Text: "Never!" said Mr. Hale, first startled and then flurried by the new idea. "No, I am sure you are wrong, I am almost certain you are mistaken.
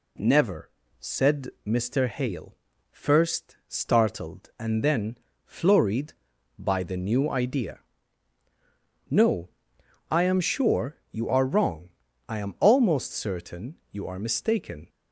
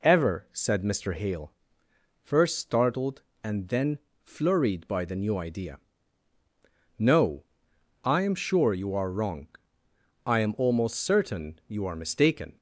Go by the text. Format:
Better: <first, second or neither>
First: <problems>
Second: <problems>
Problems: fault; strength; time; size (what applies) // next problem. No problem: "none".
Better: first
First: pauses between "then" and "flurried"; slight; at 5.1 s; 0.26 s long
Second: says "Ever" for "Never"; at 0.0 s // pauses between "then" and "flurried"; slight; at 3.9 s; 0.24 s long